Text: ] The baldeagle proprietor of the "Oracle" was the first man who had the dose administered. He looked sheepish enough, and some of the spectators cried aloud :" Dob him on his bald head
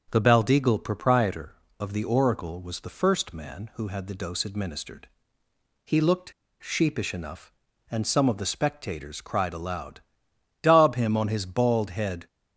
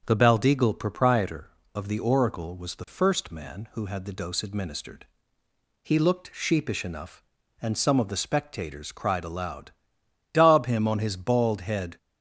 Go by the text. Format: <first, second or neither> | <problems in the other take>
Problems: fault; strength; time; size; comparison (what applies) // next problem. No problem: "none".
second | starts louder than the rest; until 1.1 s; 7 dB; strong in the second // pauses between "looked" and "sheepish"; slight; at 6.3 s; 0.29 s long